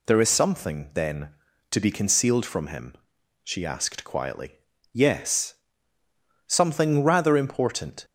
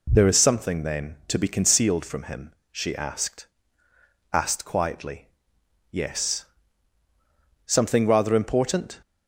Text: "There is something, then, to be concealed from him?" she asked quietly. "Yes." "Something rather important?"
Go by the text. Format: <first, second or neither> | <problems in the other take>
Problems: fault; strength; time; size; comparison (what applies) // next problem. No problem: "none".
first | says "asked" twice; at 4.3 s